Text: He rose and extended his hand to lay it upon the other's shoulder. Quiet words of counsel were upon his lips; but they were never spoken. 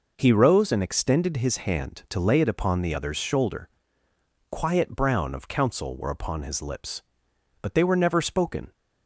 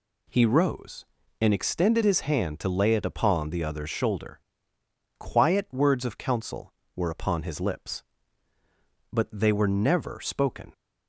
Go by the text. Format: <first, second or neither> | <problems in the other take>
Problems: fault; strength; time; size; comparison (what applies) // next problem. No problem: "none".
second | says "brown" for "words"; at 4.9 s